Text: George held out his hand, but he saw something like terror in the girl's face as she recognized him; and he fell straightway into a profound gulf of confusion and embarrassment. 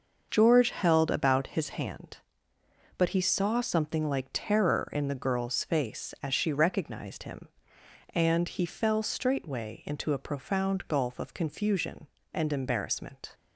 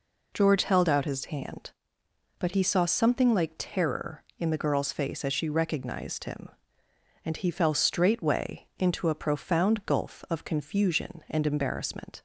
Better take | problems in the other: second | starts louder than the rest; noticeable; until 1.3 s; 6 dB // says "about" for "out"; at 1.1 s

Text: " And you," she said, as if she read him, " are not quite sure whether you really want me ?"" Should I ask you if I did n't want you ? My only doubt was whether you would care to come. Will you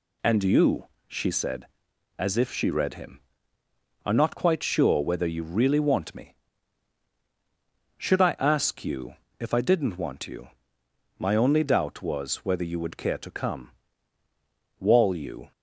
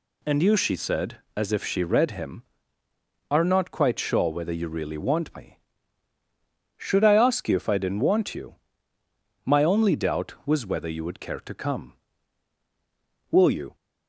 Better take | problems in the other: second | pauses between "you" and "if"; slight; at 9.1 s; 0.24 s long // says "Wall" for "Will"; at 14.7 s

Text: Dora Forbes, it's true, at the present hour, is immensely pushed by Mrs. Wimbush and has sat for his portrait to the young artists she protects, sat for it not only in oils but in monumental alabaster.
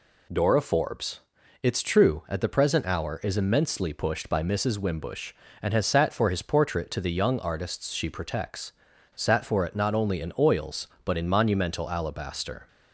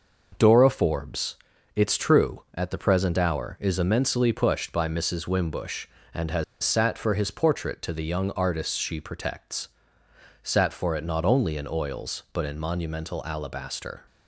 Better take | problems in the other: first | pauses between "has" and "sat"; slight; at 6.4 s; 0.19 s long

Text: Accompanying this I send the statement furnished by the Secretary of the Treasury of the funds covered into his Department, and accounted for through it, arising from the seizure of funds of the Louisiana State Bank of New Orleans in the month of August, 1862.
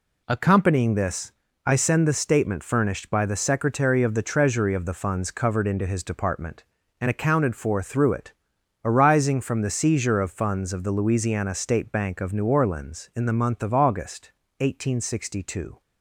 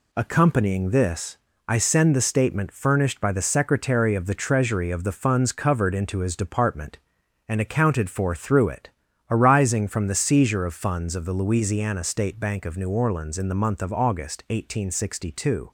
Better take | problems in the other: neither | pauses between "this" and "I"; slight; the same in both

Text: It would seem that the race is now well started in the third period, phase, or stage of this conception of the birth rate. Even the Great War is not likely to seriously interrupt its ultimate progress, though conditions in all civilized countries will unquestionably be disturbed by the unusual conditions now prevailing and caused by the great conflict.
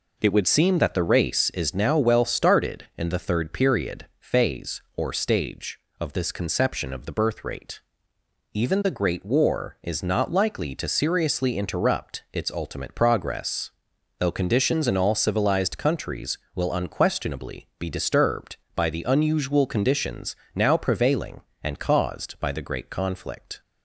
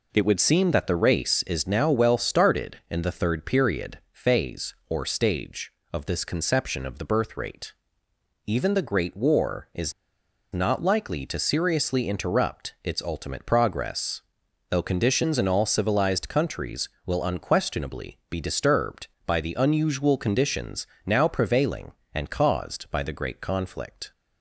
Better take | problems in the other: first | pauses between "is" and "not"; noticeable; at 9.9 s; 0.60 s long // pauses between "conditions" and "now"; slight; at 20.8 s; 0.20 s long; slight in the first

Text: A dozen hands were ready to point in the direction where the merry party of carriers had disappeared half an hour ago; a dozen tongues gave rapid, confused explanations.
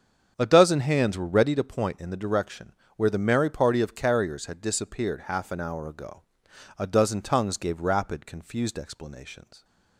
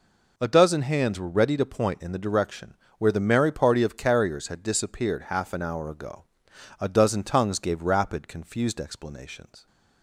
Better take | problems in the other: second | starts louder than the rest; until 1.7 s; 7 dB // pauses between "direction" and "where"; slight; at 2.7 s; 0.22 s long; slight in the second

